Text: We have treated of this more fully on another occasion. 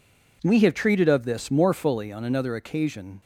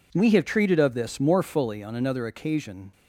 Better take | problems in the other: neither | none

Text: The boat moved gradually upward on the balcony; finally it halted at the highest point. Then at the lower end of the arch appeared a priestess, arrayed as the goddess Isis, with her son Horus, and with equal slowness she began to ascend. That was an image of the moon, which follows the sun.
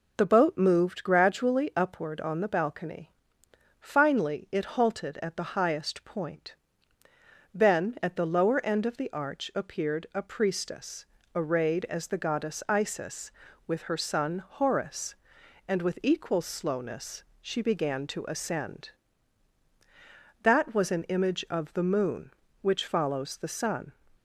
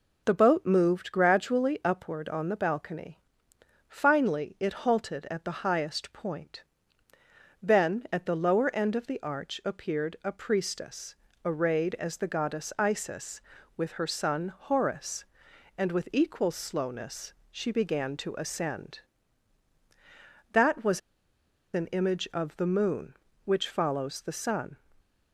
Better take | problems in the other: first | pauses between "slowness" and "she"; slight; at 17.3 s; 0.18 s long; slight in the first // pauses between "was" and "an"; noticeable; at 20.9 s; 0.74 s long

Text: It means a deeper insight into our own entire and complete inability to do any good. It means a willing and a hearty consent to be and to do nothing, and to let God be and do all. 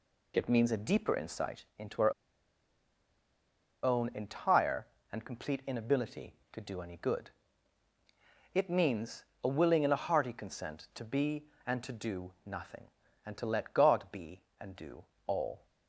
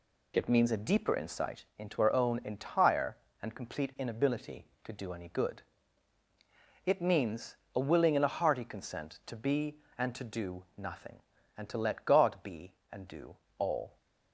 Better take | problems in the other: second | pauses between "insight" and "into"; slight; at 1.6 s; 0.16 s long; slight in the second // pauses between "our" and "own"; strong; at 2.1 s; 1.7 s long // pauses between "means" and "a"; slight; at 9.2 s; 0.20 s long; slight in the second // pauses between "do" and "all"; slight; at 15.0 s; 0.22 s long; slight in the second

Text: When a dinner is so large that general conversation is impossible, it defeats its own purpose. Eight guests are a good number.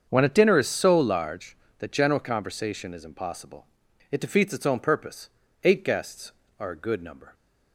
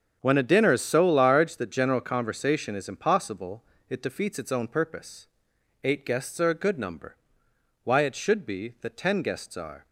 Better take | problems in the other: first | starts louder than the rest; strong; until 1.2 s; 7.5 dB; also in the first // goes on to say "Why it should be that ten guests are"; strong; from 7.8 s on; 2.0 s long

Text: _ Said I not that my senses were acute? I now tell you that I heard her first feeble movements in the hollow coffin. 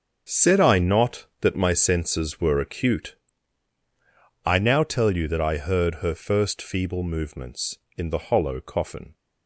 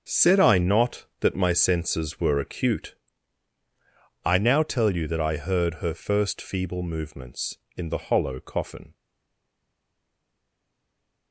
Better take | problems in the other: first | starts louder than the rest; until 1.2 s; 6.5 dB; also in the first // stays silent after the last word; from 8.9 s on; 2.4 s long

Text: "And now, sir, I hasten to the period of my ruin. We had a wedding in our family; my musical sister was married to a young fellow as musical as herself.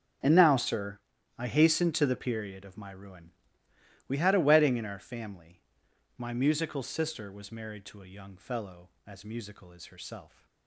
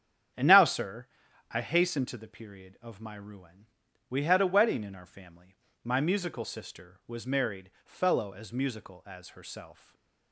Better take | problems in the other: first | starts louder than the rest; strong; until 1.8 s; 8.5 dB; also in the first // skips "to a young"; at 7.7 s // stays silent after the last word; slight; from 9.7 s on; 0.6 s long

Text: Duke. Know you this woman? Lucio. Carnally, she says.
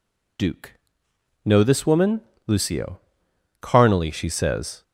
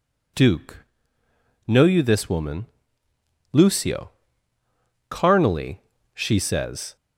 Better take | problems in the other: second | skips "you"; at 1.6 s

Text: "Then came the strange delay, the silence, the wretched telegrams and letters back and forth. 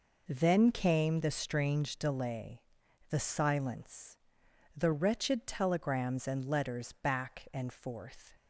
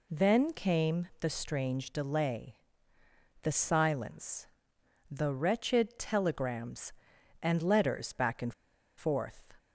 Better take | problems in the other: first | pauses between "and" and "forth"; at 8.5 s; 0.44 s long

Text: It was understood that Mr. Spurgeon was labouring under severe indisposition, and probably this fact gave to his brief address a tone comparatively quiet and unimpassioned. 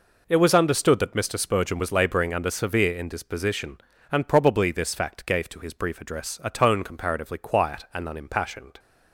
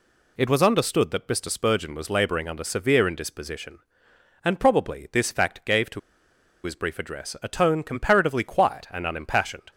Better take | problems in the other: first | pauses between "to" and "his"; noticeable; at 5.9 s; 0.64 s long

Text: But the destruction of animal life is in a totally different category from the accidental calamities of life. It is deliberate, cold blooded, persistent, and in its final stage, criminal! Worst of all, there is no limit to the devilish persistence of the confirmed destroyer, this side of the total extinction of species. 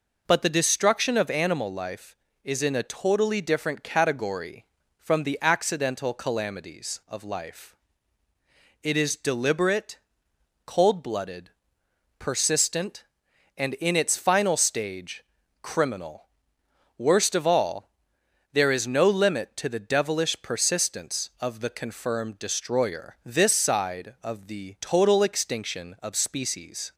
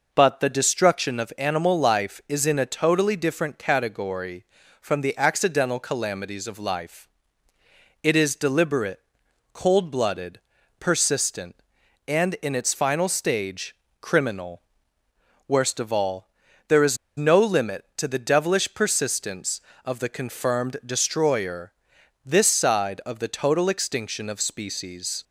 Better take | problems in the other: first | pauses between "is" and "no"; slight; at 16.9 s; 0.20 s long

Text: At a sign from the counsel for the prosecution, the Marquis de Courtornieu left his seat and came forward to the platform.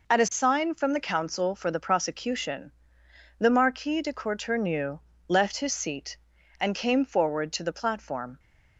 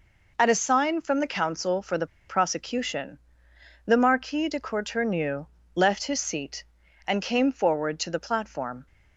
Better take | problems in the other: first | pauses between "the" and "prosecution"; slight; at 2.0 s; 0.20 s long // pauses between "Courtornieu" and "left"; slight; at 5.4 s; 0.28 s long; slight in the first

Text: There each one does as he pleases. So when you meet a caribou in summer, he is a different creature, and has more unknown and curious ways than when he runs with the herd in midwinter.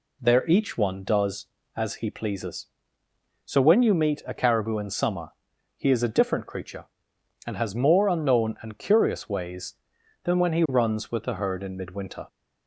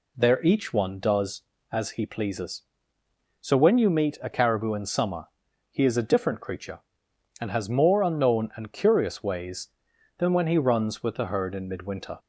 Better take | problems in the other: neither | none

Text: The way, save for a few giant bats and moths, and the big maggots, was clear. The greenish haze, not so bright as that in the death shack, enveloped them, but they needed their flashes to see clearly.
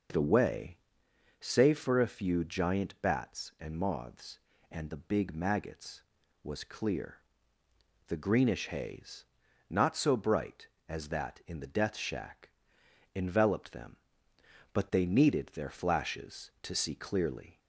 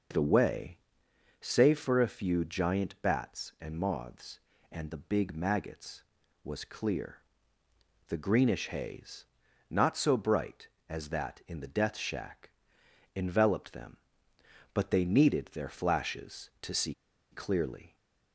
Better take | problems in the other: first | pauses between "see" and "clearly"; at 16.9 s; 0.38 s long

